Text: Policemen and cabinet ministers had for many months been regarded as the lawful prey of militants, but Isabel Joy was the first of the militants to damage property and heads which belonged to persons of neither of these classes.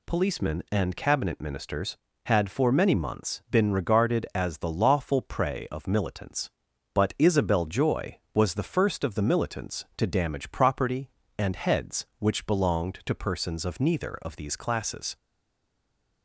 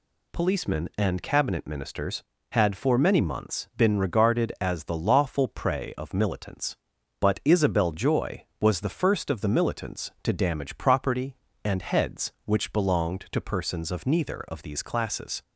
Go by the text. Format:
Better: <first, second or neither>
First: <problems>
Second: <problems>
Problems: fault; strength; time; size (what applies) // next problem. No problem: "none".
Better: second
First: stays silent after the last word; from 15.1 s on; 1.1 s long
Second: none